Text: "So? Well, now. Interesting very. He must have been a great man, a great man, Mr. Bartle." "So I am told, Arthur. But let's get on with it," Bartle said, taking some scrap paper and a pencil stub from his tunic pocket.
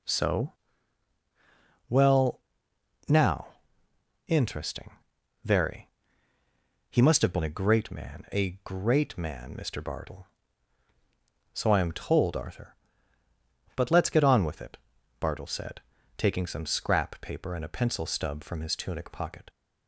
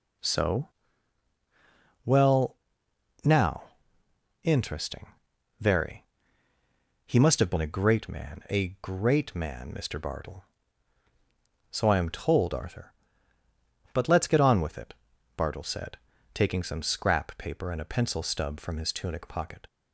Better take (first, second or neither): neither